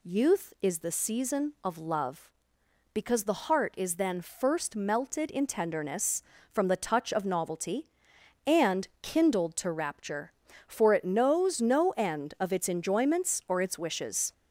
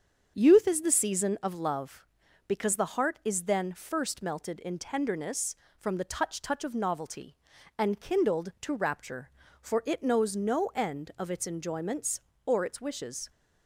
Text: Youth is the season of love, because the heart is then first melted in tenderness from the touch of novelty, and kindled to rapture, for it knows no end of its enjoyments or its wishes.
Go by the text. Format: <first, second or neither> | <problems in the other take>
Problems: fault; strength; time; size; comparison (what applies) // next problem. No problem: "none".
first | starts louder than the rest; until 1.3 s; 7 dB // says "touch" twice; at 6.4 s